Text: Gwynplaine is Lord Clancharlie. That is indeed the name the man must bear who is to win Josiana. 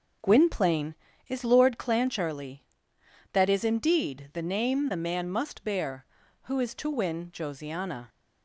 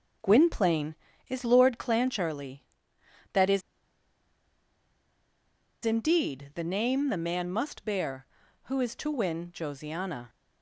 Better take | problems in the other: first | pauses between "is" and "indeed"; strong; at 3.6 s; 2.2 s long

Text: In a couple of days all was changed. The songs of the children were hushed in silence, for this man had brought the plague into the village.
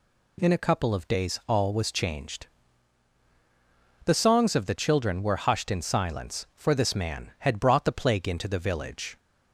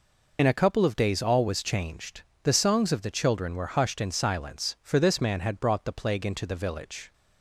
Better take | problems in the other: first | loses the start of "In"; at 0.3 s; 50 ms

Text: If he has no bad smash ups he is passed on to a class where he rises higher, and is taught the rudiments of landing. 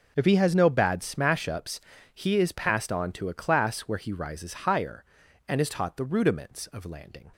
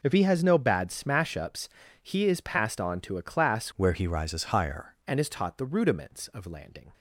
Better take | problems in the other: first | pauses between "ups" and "he"; slight; at 1.6 s; 0.32 s long; slight in the first // changes voice from "where" to "higher"; from 3.7 to 4.9 s; 1.2 s long

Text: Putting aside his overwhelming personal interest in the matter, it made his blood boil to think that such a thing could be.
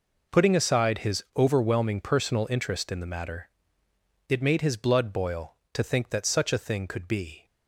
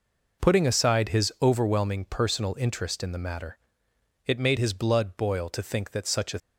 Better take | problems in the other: first | stops before "thing could be"; at 6.3 s

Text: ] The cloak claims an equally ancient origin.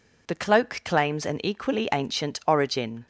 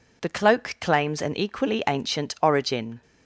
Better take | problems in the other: neither | none

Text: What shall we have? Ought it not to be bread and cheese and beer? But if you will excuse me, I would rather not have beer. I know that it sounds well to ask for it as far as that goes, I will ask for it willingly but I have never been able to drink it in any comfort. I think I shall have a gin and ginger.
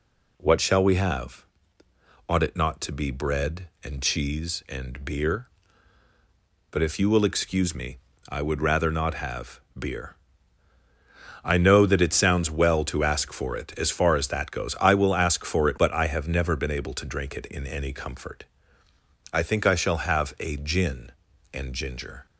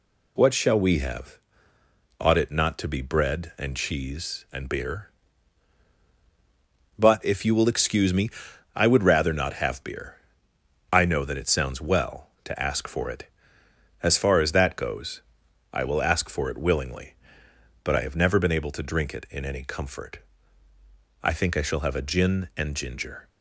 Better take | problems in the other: second | pauses between "have" and "beer"; slight; at 9.5 s; 0.18 s long // skips "willingly"; at 15.7 s

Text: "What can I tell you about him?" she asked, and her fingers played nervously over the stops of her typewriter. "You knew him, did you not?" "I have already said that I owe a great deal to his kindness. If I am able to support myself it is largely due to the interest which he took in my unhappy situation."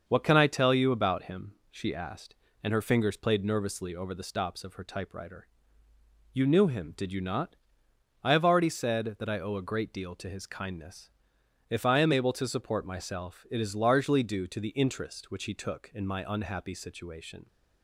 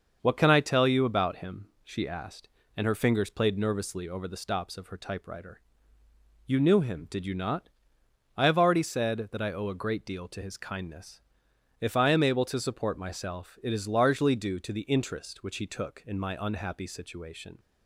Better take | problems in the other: neither | starts louder than the rest; the same in both

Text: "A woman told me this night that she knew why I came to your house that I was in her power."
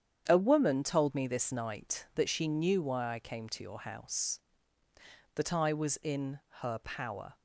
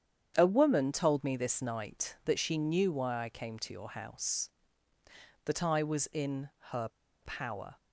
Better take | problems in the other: first | starts louder than the rest; strong; until 1.3 s; 8.5 dB; strong in the first // pauses between "in" and "her"; slight; at 6.4 s; 0.22 s long; slight in the first // pauses between "her" and "power"; slight; at 6.8 s; 0.33 s long

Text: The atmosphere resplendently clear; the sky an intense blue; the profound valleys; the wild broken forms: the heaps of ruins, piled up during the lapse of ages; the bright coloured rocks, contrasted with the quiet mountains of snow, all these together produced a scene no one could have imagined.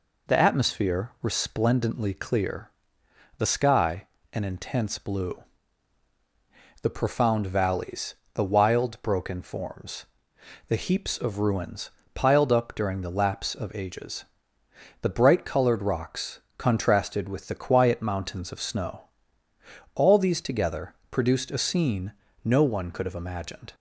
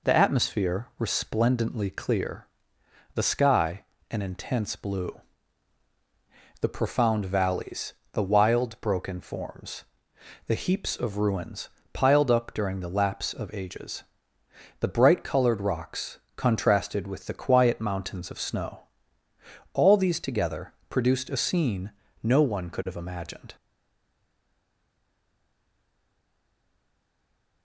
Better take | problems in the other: first | pauses between "sky" and "an"; slight; at 3.8 s; 0.26 s long; slight in the first // pauses between "together" and "produced"; slight; at 20.7 s; 0.16 s long; slight in the first // pauses between "scene" and "no"; slight; at 21.9 s; 0.30 s long; slight in the first // stays silent after the last word; strong; from 23.5 s on; 4.1 s long

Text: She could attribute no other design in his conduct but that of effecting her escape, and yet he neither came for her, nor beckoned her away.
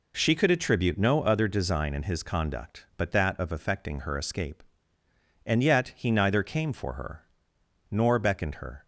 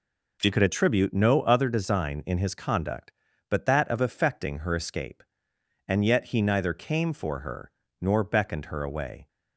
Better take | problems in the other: second | stops before "away"; at 8.8 s

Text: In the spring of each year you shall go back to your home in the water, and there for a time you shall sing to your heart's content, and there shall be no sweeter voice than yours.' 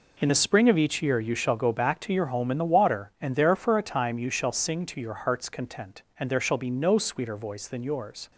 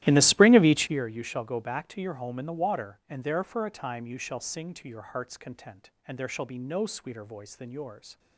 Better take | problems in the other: first | starts louder than the rest; strong; until 1.0 s; 14 dB

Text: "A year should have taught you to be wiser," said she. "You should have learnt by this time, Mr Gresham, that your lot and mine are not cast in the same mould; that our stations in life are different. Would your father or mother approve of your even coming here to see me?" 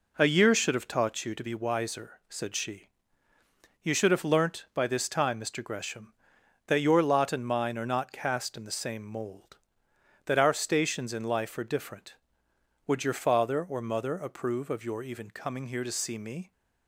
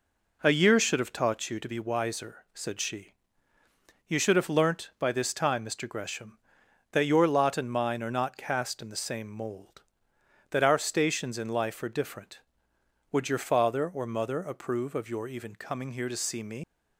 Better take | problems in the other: first | leaves "me" unfinished; at 16.6 s; 125 ms

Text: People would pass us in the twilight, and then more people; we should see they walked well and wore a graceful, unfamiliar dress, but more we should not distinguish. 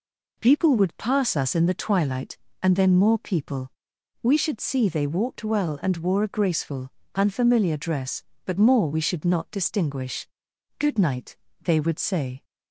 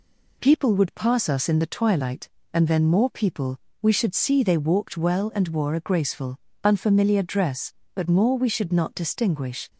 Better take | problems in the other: second | goes on to say "Good night they would say"; from 10.7 s on; 1.6 s long

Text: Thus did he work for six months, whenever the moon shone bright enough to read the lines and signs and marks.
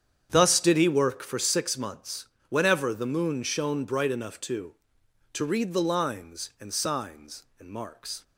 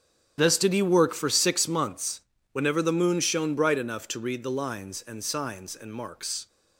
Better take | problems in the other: second | starts louder than the rest; strong; until 1.3 s; 8.5 dB; strong in the second // says "to" twice; at 5.3 s

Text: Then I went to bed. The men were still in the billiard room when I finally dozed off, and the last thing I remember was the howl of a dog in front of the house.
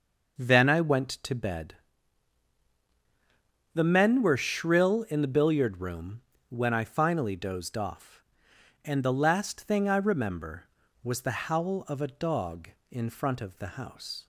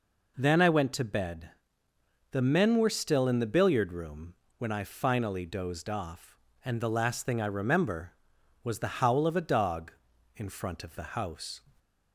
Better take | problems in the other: second | says "shrill" for "still"; at 4.3 s // pauses between "room" and "when"; slight; at 6.1 s; 0.30 s long; slight in the second

